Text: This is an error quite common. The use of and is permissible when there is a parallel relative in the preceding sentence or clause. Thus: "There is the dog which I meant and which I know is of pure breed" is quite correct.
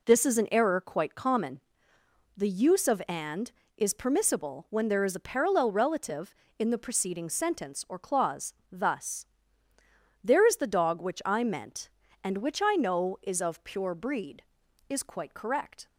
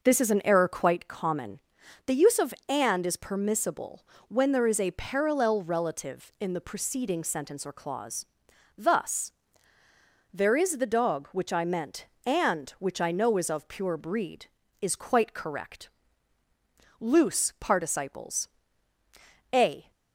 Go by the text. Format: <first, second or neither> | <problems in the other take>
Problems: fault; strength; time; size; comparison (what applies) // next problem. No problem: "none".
first | pauses between "permissible" and "when"; slight; at 4.0 s; 0.22 s long // goes on to say "LOOSE PARTICIPLES A"; strong; from 16.9 s on; 2.9 s long